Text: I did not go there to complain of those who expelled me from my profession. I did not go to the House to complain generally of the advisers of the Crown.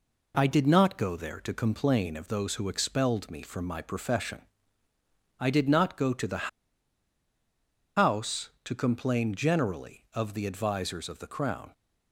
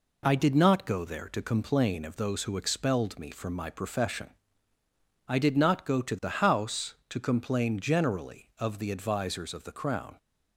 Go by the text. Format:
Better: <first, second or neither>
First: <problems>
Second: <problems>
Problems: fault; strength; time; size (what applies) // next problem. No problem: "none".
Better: second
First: pauses between "the" and "House"; strong; at 6.4 s; 1.5 s long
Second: none